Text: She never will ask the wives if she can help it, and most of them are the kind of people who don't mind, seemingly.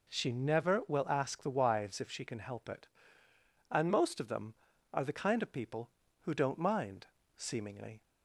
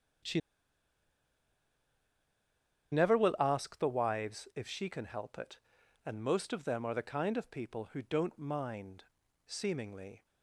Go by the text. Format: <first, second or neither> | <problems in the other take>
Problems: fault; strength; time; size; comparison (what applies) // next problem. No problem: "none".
first | starts louder than the rest; strong; until 3.8 s; 8 dB // pauses between "She" and "never"; strong; at 0.3 s; 2.5 s long